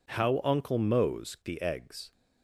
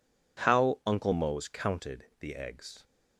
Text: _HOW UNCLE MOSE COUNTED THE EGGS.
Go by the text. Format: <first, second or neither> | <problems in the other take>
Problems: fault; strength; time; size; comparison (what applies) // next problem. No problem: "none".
second | skips "COUNTED"; at 1.3 s